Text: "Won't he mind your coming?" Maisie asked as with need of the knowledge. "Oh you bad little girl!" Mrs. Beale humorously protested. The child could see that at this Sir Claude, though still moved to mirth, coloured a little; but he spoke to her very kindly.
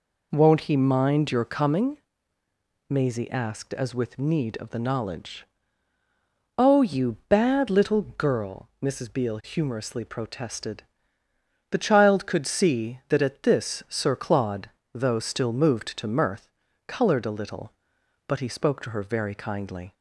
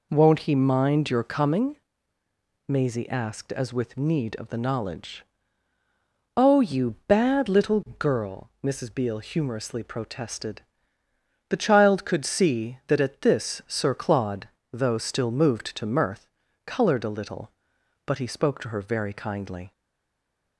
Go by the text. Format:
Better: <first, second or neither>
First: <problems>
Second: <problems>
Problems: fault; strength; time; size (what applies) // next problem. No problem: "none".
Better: first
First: none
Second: stays silent after the last word; slight; from 19.7 s on; 0.8 s long